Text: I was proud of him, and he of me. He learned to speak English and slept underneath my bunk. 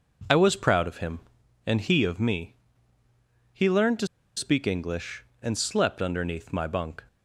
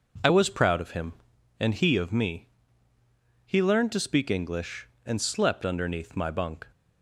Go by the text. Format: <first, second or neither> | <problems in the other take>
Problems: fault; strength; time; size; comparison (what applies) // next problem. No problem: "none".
second | pauses between "to" and "speak"; slight; at 4.0 s; 0.30 s long